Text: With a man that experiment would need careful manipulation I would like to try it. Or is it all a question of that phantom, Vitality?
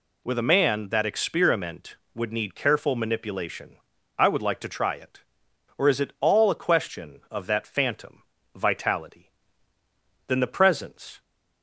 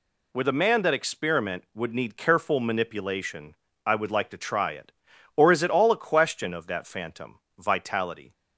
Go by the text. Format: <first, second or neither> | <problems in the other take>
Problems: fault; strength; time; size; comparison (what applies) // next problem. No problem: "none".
second | pauses between "manipulation" and "I"; at 3.7 s; 0.40 s long; slight in the second // goes on to say "Then the presence"; noticeable; from 10.2 s on; 0.94 s long